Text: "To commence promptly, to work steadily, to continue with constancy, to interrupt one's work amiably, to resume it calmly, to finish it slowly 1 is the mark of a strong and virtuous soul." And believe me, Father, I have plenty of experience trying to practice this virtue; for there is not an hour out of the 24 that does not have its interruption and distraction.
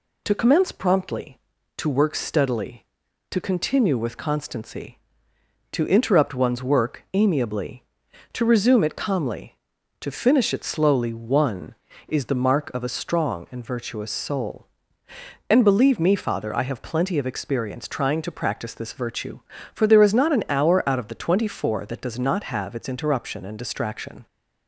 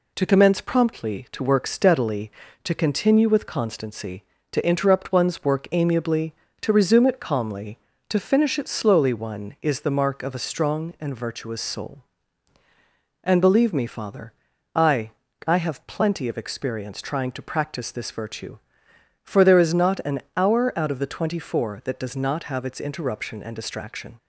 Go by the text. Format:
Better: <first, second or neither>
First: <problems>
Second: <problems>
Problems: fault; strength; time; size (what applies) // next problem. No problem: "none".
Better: first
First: none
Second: says "I" twice; at 15.4 s